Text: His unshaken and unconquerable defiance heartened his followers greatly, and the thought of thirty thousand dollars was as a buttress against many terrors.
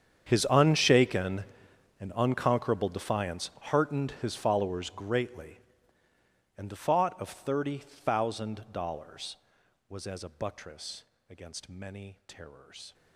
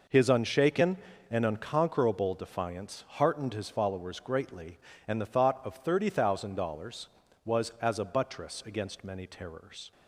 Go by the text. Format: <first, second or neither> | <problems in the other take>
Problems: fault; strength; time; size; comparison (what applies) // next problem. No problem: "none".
second | gets quieter; strong; throughout; 20.5 dB // pauses between "buttress" and "against"; slight; at 11.0 s; 0.24 s long